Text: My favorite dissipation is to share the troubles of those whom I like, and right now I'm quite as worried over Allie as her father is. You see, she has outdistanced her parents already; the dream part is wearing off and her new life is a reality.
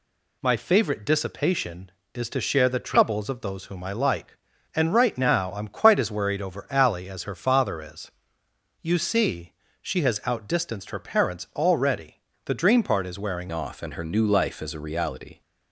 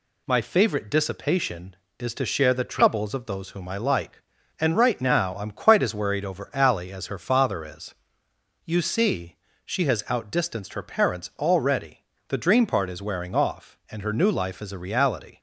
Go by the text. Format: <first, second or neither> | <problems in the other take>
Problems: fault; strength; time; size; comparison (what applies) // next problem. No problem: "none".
second | changes voice at "off"; from 13.5 s on; 1.9 s long